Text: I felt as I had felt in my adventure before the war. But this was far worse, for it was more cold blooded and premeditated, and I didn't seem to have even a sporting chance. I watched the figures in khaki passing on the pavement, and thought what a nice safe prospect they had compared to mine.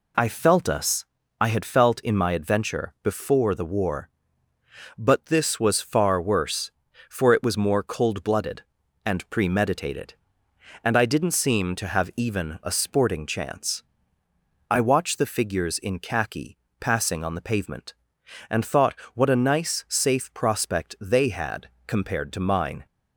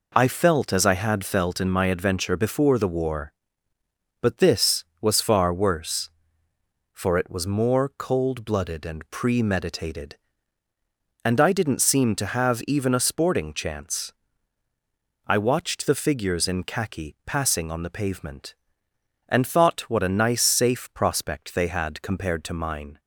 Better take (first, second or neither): second